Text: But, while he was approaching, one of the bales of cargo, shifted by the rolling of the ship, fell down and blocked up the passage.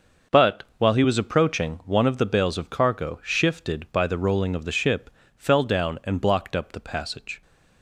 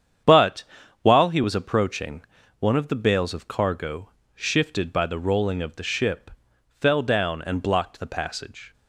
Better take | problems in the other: first | starts louder than the rest; strong; until 1.6 s; 8.5 dB; also in the first // skips "up"; at 7.9 s

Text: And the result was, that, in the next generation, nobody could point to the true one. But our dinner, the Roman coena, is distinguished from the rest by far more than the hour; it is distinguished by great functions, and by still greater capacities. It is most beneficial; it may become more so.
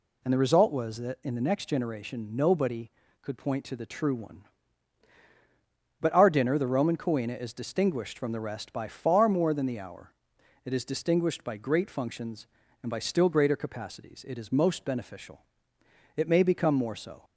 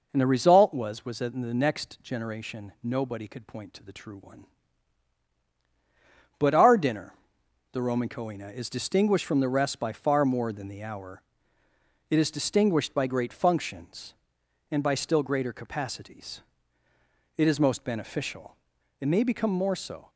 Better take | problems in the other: first | says "was" twice; at 1.0 s

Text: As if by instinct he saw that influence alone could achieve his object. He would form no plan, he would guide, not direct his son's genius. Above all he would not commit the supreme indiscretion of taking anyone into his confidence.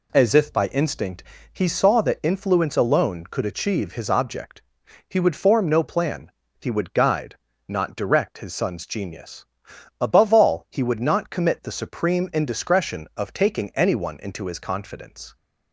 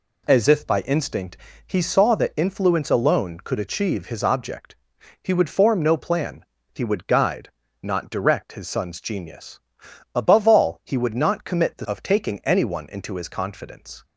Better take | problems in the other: first | pauses between "instinct" and "he"; slight; at 1.3 s; 0.32 s long; slight in the first // skips "supreme indiscretion"; at 11.8 s

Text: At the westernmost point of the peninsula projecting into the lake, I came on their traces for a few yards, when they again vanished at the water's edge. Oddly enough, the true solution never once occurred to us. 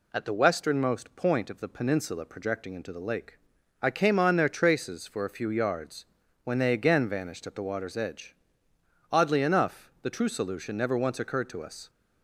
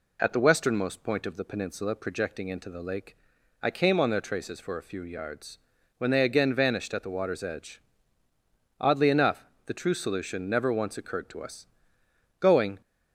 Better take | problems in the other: first | goes on to say "Going"; slight; from 12.3 s on; 0.42 s long

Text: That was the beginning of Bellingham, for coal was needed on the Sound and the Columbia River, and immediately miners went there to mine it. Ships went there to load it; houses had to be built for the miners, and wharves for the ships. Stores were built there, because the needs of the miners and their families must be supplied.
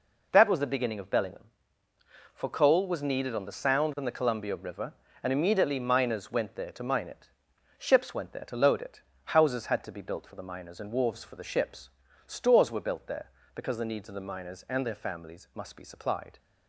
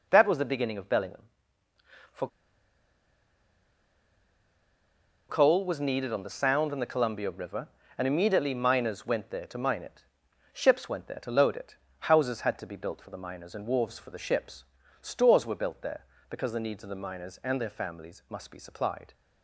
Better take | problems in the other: first | pauses between "for" and "coal"; strong; at 2.2 s; 3.0 s long

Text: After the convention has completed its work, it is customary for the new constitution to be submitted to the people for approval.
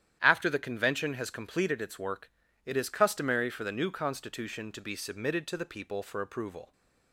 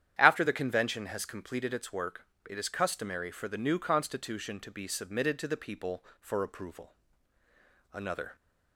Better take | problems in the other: first | starts louder than the rest; strong; until 1.2 s; 10 dB; strong in the first // goes on to say "Another"; slight; from 7.9 s on; 0.44 s long

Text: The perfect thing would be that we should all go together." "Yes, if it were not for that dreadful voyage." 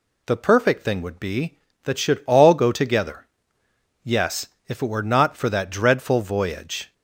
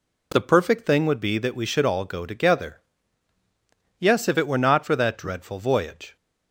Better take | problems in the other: second | skips "we"; at 1.9 s

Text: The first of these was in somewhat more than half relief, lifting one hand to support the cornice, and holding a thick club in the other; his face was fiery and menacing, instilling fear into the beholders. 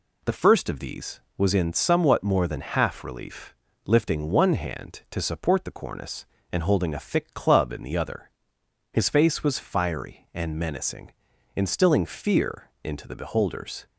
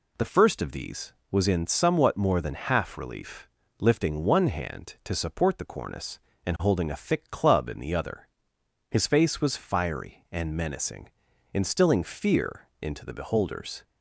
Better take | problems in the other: neither | none

